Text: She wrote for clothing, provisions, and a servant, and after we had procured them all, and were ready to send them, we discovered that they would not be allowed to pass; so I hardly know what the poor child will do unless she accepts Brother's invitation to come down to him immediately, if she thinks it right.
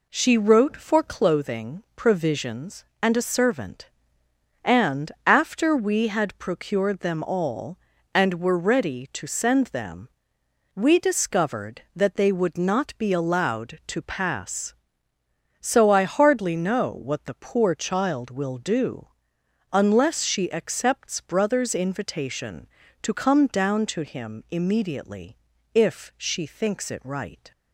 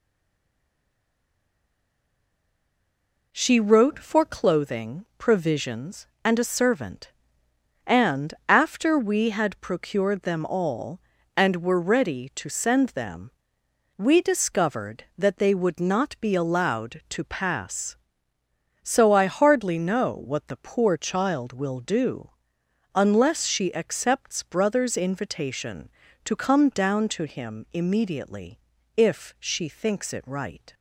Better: first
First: pauses between "and" and "after"; slight; at 5.1 s; 0.16 s long // pauses between "do" and "unless"; noticeable; at 19.0 s; 0.66 s long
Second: stays silent before the first word; strong; until 3.3 s; 3.3 s long // pauses between "and" and "after"; slight; at 8.3 s; 0.16 s long // pauses between "do" and "unless"; noticeable; at 22.2 s; 0.66 s long

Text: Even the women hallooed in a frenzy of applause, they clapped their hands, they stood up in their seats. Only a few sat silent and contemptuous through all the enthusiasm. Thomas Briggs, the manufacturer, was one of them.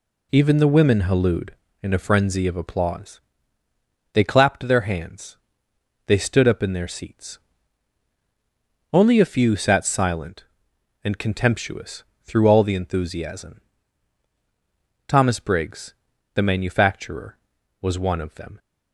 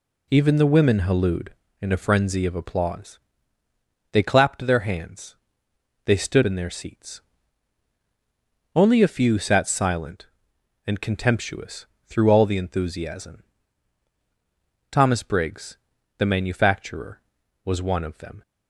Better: first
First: pauses between "contemptuous" and "through"; slight; at 12.0 s; 0.18 s long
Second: skips "up"; at 6.4 s // pauses between "contemptuous" and "through"; slight; at 11.8 s; 0.18 s long

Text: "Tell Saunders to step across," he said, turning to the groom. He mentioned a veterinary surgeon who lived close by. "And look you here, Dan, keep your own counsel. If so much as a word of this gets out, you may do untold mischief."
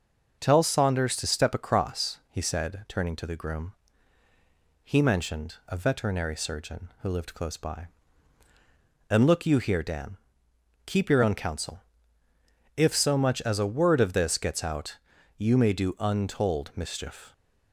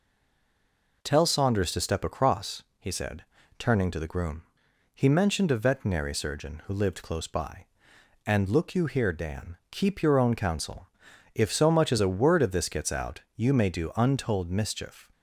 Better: first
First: none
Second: stays silent before the first word; until 1.0 s; 1.0 s long

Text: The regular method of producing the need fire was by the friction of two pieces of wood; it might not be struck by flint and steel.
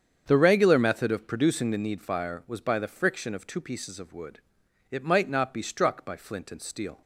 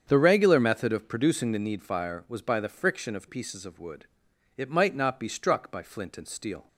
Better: first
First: starts louder than the rest; strong; until 1.2 s; 8 dB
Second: starts louder than the rest; strong; until 1.0 s; 7.5 dB // skips "two"; at 3.2 s

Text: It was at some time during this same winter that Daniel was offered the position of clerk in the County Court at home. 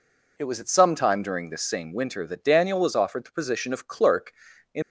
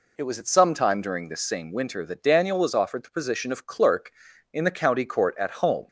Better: second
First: stops before "the County Court at home"; at 4.8 s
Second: none

